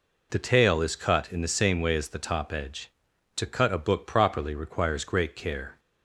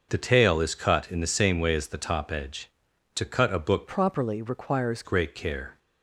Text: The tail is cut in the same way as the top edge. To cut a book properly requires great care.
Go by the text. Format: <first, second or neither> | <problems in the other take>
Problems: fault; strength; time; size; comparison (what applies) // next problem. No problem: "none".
first | starts louder than the rest; until 1.1 s; 6 dB // changes voice from "properly" to "requires"; from 3.8 to 5.0 s; 1.2 s long